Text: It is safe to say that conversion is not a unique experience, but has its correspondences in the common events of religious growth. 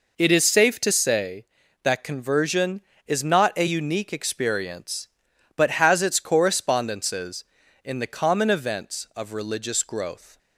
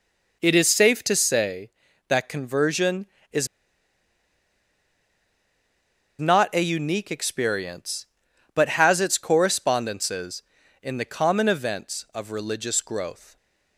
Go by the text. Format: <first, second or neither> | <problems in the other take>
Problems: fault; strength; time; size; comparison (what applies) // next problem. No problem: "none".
first | pauses between "is" and "not"; strong; at 3.4 s; 2.7 s long